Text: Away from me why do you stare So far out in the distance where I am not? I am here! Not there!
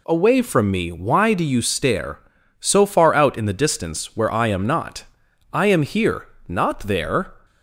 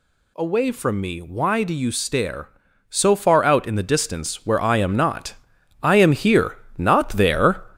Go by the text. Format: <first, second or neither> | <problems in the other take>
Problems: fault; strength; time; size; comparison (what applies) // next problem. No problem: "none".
first | gets louder; noticeable; throughout; 5 dB